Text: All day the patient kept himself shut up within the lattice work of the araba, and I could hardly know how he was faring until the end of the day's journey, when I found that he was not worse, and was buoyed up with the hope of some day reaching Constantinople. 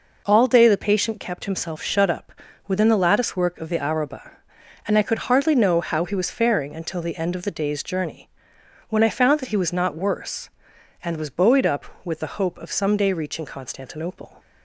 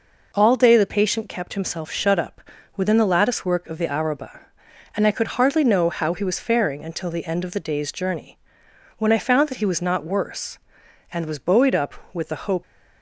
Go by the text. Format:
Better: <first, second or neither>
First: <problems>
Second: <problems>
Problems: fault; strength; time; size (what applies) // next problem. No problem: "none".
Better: first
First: pauses between "up" and "within"; slight; at 2.3 s; 0.34 s long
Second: pauses between "up" and "within"; slight; at 2.4 s; 0.34 s long // stops before "of some day reaching Constantinople"; at 12.6 s